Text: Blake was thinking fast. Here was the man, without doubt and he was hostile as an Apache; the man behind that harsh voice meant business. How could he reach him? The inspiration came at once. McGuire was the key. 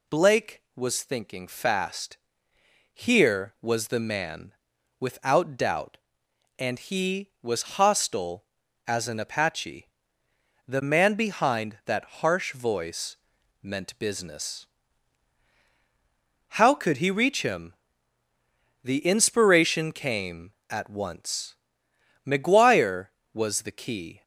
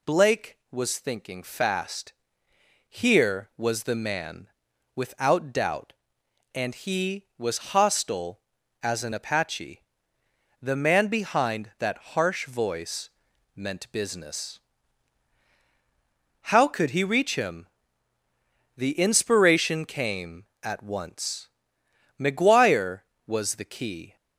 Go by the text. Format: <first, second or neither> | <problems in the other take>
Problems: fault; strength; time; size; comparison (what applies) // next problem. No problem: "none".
neither | pauses between "voice" and "meant"; noticeable; the same in both